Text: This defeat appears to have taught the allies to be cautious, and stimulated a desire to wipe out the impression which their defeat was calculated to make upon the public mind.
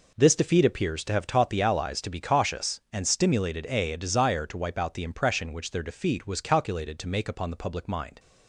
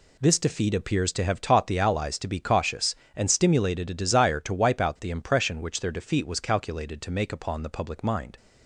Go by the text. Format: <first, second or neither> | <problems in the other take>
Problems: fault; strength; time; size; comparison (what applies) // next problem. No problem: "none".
second | says "a" twice; at 3.9 s